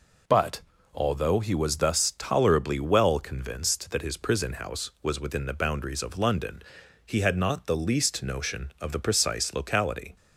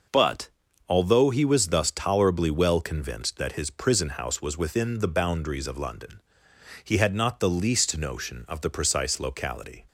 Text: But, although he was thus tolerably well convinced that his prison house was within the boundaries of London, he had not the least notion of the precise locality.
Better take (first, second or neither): neither